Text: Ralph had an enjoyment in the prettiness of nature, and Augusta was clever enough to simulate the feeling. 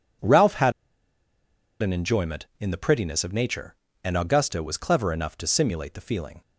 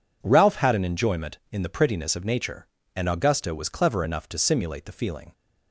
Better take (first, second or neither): second